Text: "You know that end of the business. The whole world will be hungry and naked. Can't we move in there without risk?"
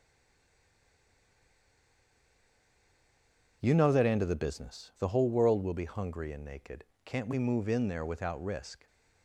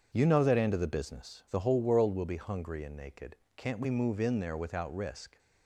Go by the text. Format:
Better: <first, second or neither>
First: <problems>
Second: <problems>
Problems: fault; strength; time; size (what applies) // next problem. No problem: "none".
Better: second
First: stays silent before the first word; strong; until 3.6 s; 3.6 s long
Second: none